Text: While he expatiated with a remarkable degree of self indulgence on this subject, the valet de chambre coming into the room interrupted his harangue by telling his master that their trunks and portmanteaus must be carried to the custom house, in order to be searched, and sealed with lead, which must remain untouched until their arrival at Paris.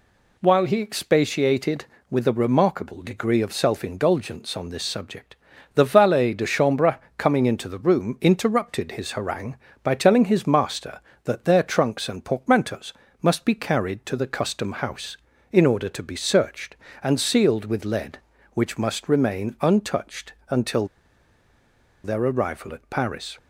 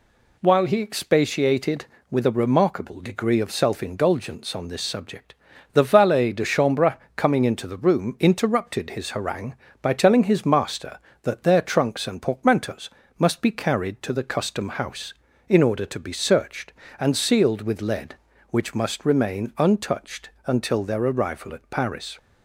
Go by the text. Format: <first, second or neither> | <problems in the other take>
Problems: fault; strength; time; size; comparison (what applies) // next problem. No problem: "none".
second | pauses between "chambre" and "coming"; slight; at 6.9 s; 0.18 s long; slight in the second // pauses between "portmanteaus" and "must"; slight; at 12.9 s; 0.30 s long; slight in the second // pauses between "untouched" and "until"; slight; at 20.3 s; 0.18 s long; slight in the second // pauses between "until" and "their"; at 20.8 s; 1.1 s long